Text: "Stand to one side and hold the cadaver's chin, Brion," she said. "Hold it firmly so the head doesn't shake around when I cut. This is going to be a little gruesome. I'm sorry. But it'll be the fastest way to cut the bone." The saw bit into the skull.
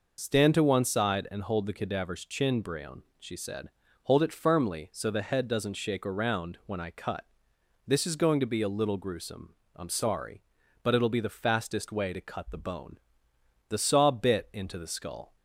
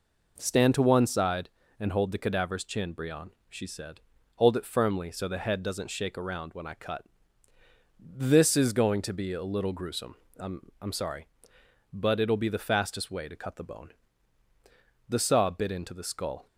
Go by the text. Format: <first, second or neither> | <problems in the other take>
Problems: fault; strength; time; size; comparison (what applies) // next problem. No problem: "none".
first | says "I'm" twice; at 10.7 s